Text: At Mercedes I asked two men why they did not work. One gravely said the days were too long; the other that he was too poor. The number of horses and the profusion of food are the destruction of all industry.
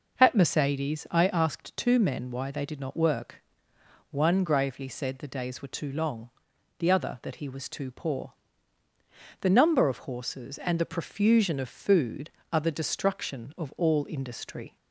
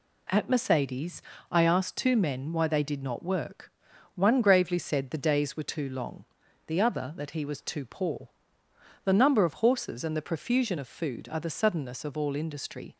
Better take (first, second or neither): first